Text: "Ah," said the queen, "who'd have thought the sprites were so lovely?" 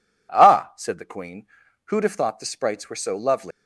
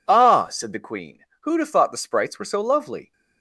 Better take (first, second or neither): second